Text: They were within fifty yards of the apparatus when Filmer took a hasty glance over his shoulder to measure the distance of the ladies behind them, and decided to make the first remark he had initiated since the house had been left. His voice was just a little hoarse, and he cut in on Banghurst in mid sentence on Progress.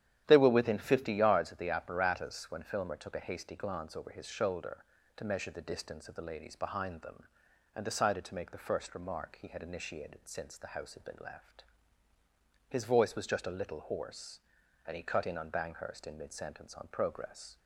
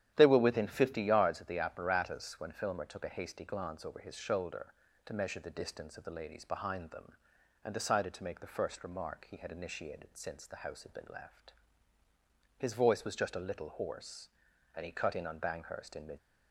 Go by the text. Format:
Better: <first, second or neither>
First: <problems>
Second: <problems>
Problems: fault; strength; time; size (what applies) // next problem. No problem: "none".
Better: first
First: starts louder than the rest; strong; until 1.2 s; 10.5 dB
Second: starts louder than the rest; strong; until 1.1 s; 10.5 dB // stops before "sentence on Progress"; at 16.1 s